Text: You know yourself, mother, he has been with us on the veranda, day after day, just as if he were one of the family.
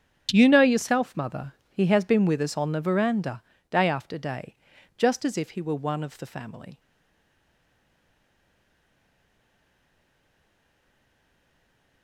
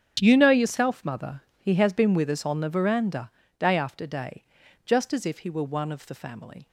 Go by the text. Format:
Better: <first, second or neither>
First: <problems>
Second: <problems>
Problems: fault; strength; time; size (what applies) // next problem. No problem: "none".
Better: second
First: starts louder than the rest; strong; until 1.3 s; 8.5 dB // stays silent after the last word; strong; from 6.7 s on; 5.3 s long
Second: starts louder than the rest; strong; until 1.2 s; 8.5 dB